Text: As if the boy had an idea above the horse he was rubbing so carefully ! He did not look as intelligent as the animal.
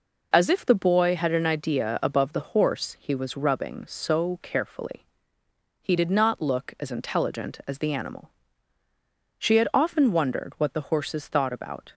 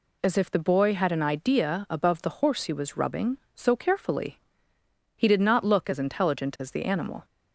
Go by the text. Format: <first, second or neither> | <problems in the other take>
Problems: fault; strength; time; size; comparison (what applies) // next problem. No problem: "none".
second | goes on to say "She had often wondered what the horses thought about"; strong; from 9.3 s on; 2.5 s long